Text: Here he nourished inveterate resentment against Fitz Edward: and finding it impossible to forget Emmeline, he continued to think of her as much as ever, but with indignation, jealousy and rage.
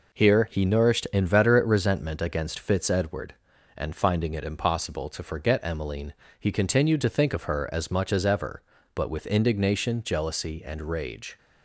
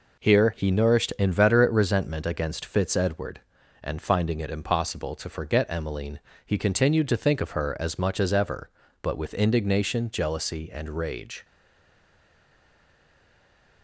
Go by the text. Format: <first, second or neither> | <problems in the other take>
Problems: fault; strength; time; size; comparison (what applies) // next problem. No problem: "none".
first | stays silent after the last word; from 11.4 s on; 2.4 s long